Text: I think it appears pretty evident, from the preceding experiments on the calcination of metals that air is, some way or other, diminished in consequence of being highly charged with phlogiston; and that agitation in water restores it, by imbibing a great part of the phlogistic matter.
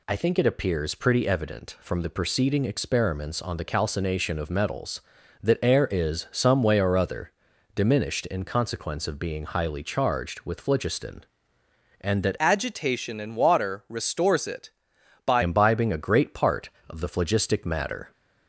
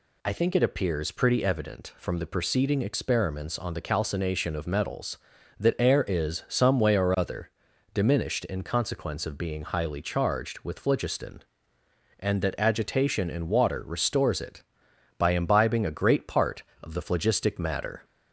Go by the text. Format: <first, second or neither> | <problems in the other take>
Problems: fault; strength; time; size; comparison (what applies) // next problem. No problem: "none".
second | changes voice from "agitation" to "by"; from 12.4 to 15.4 s; 3.0 s long